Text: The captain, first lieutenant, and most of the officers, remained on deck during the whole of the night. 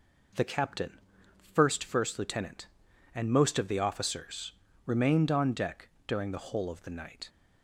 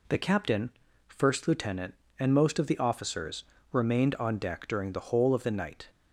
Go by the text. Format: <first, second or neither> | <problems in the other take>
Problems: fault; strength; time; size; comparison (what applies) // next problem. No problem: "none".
second | says "first" twice; at 1.8 s // pauses between "deck" and "during"; slight; at 5.8 s; 0.18 s long